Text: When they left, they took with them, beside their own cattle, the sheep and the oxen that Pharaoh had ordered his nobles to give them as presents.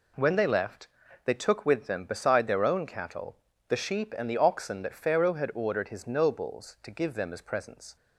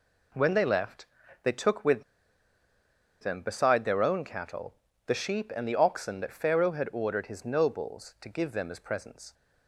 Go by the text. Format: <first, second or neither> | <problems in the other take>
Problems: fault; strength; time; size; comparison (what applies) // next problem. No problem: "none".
first | pauses between "with" and "them"; at 2.0 s; 1.1 s long